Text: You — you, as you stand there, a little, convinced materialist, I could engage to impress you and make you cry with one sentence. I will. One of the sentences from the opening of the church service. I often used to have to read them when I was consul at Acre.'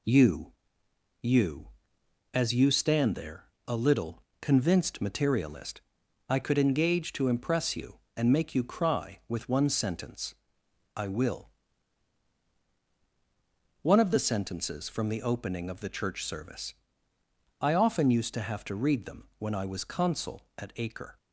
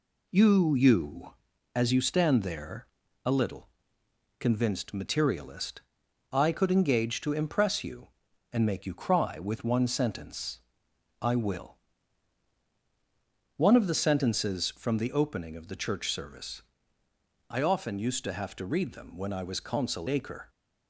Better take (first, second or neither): first